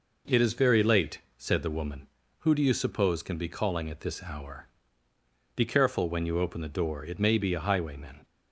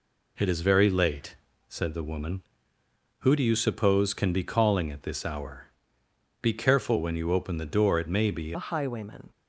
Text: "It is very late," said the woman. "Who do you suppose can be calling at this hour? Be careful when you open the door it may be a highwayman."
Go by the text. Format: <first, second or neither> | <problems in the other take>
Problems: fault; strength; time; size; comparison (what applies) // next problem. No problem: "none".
first | changes voice at "a"; from 8.5 s on; 0.8 s long